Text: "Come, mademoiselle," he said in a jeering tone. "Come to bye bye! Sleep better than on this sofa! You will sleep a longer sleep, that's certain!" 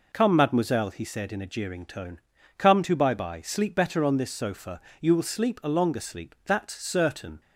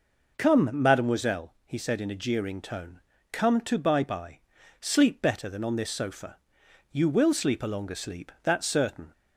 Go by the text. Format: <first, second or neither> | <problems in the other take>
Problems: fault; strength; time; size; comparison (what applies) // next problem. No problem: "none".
second | skips "than"; at 4.0 s